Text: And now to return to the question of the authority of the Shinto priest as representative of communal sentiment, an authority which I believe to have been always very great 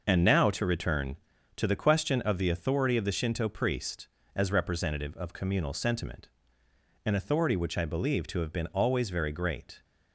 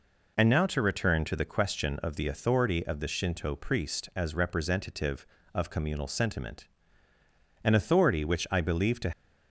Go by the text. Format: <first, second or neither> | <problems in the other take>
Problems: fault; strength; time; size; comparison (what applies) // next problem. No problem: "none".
first | stops before "have been always very great"; at 9.1 s